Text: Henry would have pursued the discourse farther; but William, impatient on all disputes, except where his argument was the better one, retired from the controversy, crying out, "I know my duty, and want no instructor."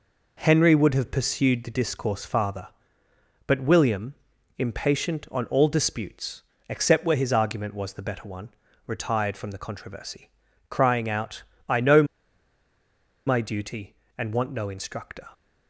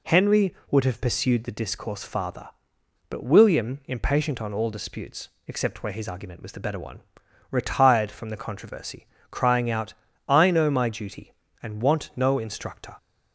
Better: second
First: pauses between "know" and "my"; at 12.0 s; 1.2 s long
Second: none

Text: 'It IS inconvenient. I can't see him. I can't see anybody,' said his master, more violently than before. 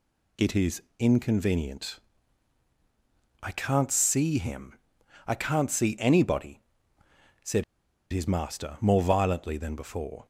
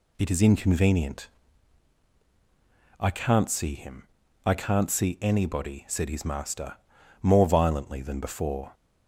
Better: second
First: pauses between "IS" and "inconvenient"; slight; at 0.8 s; 0.18 s long // pauses between "said" and "his"; noticeable; at 7.6 s; 0.49 s long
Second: none

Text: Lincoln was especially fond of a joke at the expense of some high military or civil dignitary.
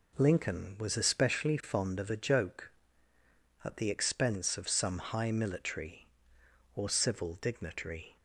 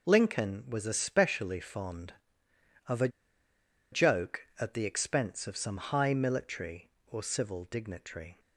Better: first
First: none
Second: pauses between "a" and "joke"; noticeable; at 3.0 s; 0.83 s long

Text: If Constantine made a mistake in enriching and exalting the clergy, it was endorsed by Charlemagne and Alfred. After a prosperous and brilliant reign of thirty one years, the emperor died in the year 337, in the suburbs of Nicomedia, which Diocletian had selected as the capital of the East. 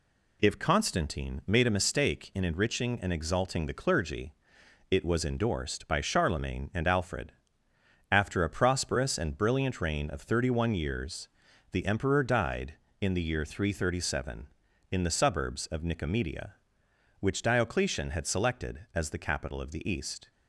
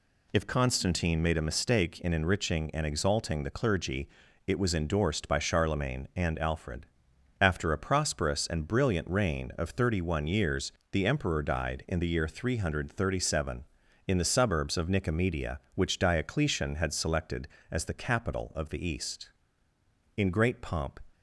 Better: first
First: none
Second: goes on to say "In great pomp"; noticeable; from 20.1 s on; 0.82 s long

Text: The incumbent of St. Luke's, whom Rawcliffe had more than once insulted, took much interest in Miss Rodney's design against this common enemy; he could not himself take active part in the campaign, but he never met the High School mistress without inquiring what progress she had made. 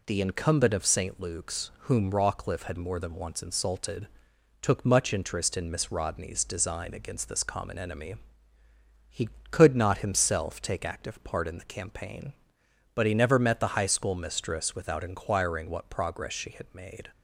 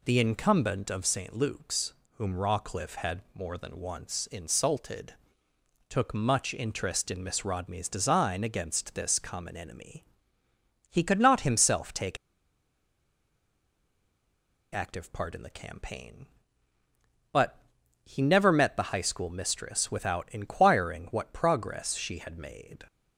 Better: first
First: none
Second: pauses between "take" and "active"; strong; at 12.1 s; 2.5 s long // pauses between "but" and "he"; at 17.6 s; 0.42 s long

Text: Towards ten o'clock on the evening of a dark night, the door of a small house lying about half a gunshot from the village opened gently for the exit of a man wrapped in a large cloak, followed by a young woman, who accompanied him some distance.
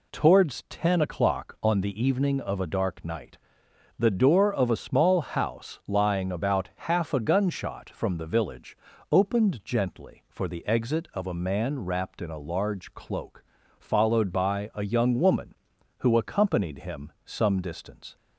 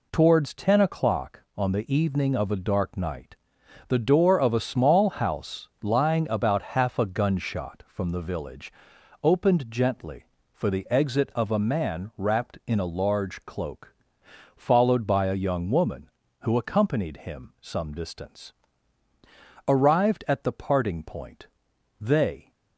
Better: first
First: pauses between "village" and "opened"; slight; at 8.7 s; 0.34 s long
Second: pauses between "house" and "lying"; slight; at 5.6 s; 0.16 s long // pauses between "village" and "opened"; noticeable; at 8.7 s; 0.50 s long // goes on to say "Arrived at the parting point they"; strong; from 19.6 s on; 2.8 s long

